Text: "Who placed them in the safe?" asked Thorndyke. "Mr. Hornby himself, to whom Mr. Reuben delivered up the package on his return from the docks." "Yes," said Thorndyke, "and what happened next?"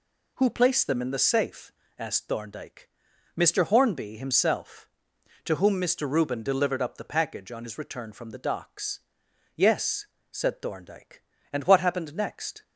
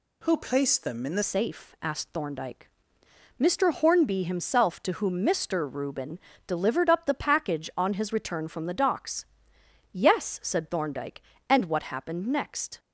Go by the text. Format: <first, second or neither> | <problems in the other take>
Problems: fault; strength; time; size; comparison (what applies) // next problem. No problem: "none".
first | changes voice at "safe"; from 1.2 s on; 11.5 s long // pauses between "Reuben" and "delivered"; slight; at 6.1 s; 0.30 s long